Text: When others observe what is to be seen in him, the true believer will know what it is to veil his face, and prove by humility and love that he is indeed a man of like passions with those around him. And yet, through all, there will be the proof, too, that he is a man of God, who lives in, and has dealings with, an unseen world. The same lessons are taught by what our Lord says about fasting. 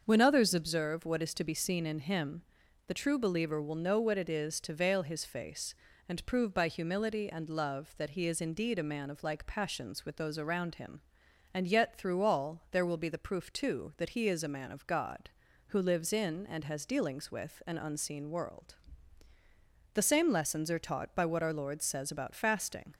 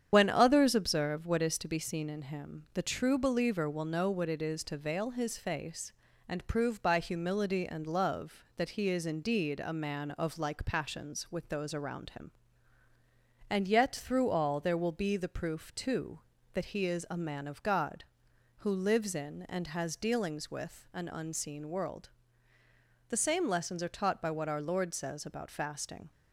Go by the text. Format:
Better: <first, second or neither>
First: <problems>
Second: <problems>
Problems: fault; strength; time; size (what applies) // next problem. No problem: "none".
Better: first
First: starts louder than the rest; until 1.0 s; 6.5 dB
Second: loses the start of "When"; at 0.1 s; 40 ms // starts louder than the rest; strong; until 1.1 s; 8.5 dB